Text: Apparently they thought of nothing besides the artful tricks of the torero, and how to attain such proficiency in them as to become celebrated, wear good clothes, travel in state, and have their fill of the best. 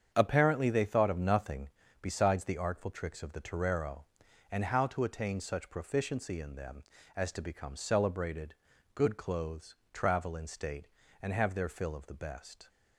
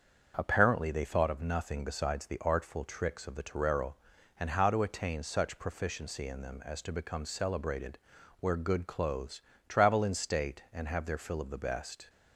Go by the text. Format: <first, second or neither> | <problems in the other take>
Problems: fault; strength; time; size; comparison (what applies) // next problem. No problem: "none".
second | starts louder than the rest; strong; until 1.1 s; 8 dB; also in the second // pauses between "nothing" and "besides"; slight; at 1.6 s; 0.32 s long // skips "wear"; at 8.7 s